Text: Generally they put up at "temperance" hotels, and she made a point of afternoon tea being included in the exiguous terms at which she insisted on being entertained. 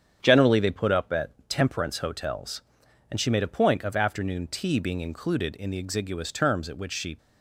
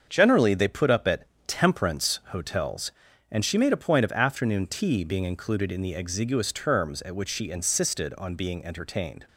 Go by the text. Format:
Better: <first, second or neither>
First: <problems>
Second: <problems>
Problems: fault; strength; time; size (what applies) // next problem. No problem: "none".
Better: second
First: starts louder than the rest; strong; until 1.2 s; 8 dB // pauses between "at" and "temperance"; slight; at 1.3 s; 0.18 s long // stops before "insisted on being entertained"; at 7.1 s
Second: starts louder than the rest; until 1.0 s; 7 dB // pauses between "at" and "temperance"; slight; at 1.2 s; 0.18 s long